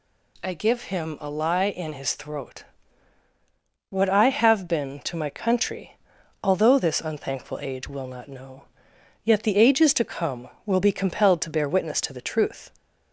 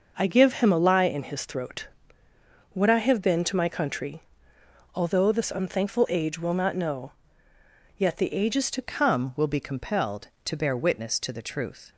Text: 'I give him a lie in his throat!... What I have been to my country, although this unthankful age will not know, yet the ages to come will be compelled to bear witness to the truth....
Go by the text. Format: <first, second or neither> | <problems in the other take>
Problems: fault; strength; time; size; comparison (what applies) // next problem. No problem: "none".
first | changes voice at "come"; from 8.8 s on; 3.1 s long